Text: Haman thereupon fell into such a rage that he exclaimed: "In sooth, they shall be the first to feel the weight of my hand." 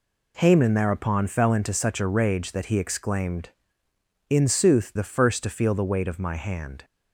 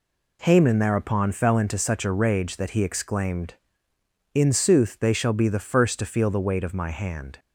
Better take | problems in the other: second | skips "they shall be"; at 4.9 s

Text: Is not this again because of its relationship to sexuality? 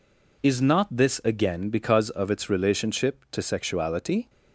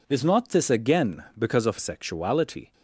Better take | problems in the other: first | skips "its relationship to"; at 1.7 s

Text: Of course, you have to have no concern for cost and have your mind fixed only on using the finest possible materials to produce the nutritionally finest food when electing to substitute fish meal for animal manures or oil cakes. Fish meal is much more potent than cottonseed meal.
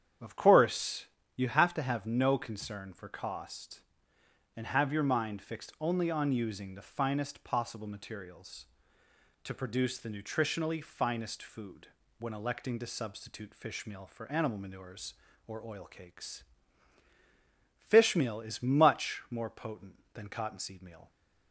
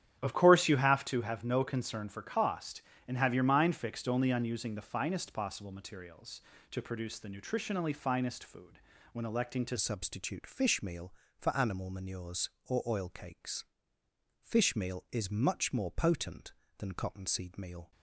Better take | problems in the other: first | starts louder than the rest; strong; until 1.2 s; 10 dB; strong in the first // pauses between "food" and "when"; slight; at 8.7 s; 0.34 s long; slight in the first // changes voice at "substitute"; from 9.7 s on; 8.2 s long

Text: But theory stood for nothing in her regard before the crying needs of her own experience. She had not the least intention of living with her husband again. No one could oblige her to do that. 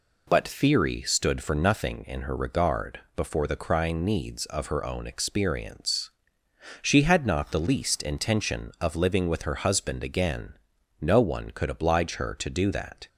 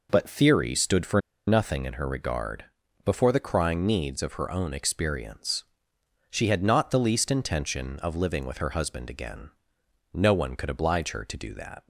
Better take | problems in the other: first | pauses between "for" and "nothing"; slight; at 1.2 s; 0.26 s long // pauses between "regard" and "before"; at 2.6 s; 0.40 s long; slight in the first

